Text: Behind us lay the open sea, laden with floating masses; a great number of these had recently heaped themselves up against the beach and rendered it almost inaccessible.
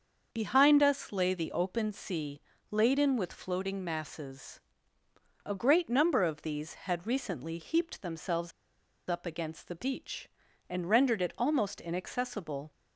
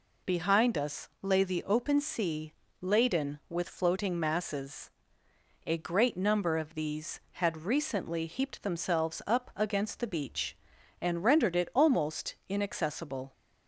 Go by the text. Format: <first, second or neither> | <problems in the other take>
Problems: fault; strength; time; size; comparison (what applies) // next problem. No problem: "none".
second | starts louder than the rest; until 1.3 s; 6.5 dB // pauses between "themselves" and "up"; noticeable; at 8.5 s; 0.58 s long